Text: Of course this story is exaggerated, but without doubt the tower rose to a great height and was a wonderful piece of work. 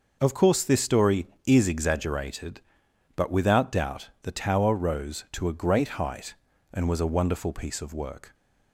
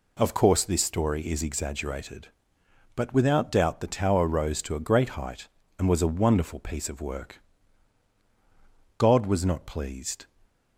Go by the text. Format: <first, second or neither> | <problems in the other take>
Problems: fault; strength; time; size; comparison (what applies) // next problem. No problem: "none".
first | goes on to say "God was not pleased"; noticeable; from 8.9 s on; 1.2 s long